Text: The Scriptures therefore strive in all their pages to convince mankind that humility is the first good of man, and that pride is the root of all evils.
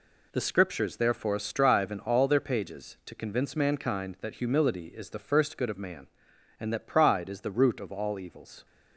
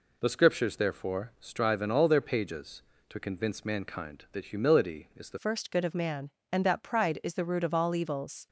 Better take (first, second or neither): first